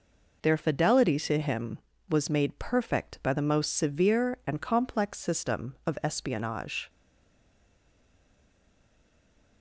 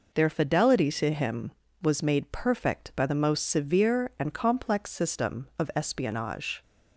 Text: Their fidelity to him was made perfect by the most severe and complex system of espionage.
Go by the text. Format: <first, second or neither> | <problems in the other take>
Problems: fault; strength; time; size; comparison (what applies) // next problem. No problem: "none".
second | stays silent after the last word; strong; from 6.8 s on; 2.8 s long